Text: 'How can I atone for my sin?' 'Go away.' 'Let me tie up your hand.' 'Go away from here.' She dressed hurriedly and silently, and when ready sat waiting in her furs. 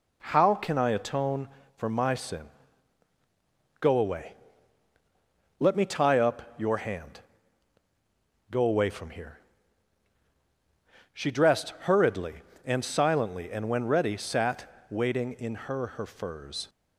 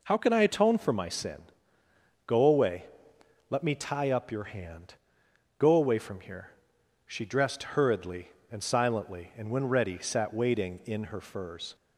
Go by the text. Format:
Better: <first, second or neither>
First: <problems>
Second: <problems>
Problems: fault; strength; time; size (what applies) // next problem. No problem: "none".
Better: second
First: pauses between "sat" and "waiting"; slight; at 14.6 s; 0.22 s long // says "her" twice; at 15.8 s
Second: none